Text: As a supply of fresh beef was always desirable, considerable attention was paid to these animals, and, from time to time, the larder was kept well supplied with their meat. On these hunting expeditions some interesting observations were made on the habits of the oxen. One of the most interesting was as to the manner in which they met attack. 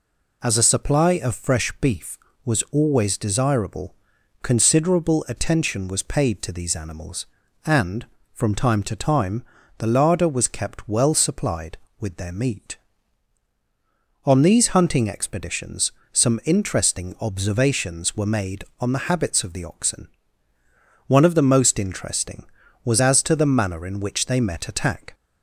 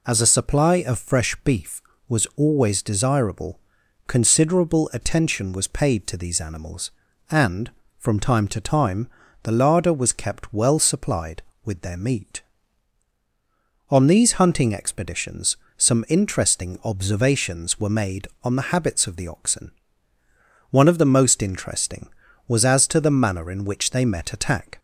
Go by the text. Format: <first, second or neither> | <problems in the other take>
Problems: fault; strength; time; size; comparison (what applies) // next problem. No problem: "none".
neither | pauses between "expeditions" and "some"; slight; the same in both